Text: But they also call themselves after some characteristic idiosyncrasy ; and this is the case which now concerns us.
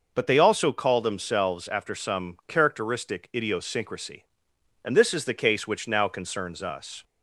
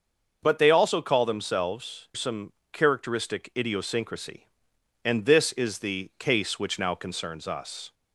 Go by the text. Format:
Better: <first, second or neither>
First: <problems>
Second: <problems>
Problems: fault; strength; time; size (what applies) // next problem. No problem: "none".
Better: first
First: none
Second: starts louder than the rest; until 1.4 s; 6.5 dB // skips "after"; at 2.1 s // pauses between "some" and "characteristic"; slight; at 2.5 s; 0.20 s long